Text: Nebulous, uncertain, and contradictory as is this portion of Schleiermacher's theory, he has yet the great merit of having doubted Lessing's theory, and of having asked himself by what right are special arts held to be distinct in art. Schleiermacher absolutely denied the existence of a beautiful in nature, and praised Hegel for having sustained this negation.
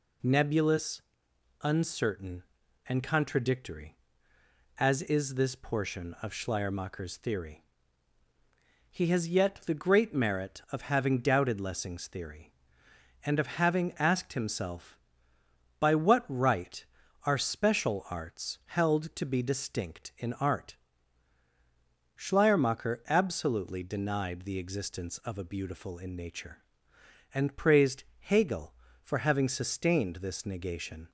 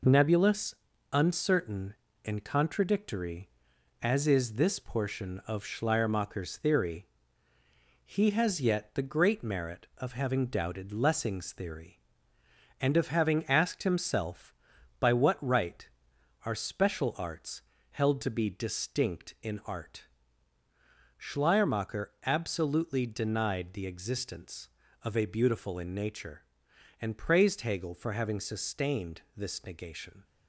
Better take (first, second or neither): first